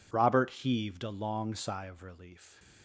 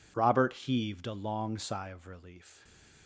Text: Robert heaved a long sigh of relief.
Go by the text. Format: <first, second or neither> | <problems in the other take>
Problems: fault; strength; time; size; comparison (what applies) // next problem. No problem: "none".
neither | stays silent after the last word; slight; the same in both